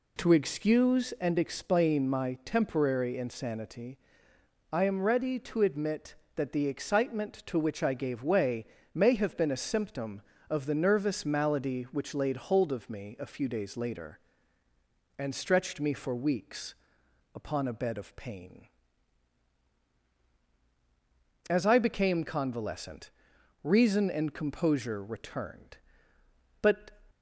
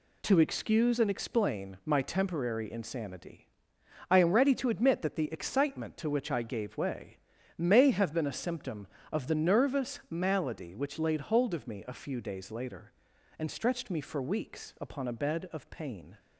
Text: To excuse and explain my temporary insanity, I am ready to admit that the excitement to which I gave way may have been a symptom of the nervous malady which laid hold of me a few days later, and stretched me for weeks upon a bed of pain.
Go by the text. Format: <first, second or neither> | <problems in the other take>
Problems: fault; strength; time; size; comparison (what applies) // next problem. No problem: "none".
second | pauses between "way" and "may"; slight; at 8.6 s; 0.30 s long; also in the second // pauses between "weeks" and "upon"; noticeable; at 16.7 s; 0.62 s long // goes on to say "As I became convalescent reason and composure returned But"; strong; from 21.4 s on; 5.4 s long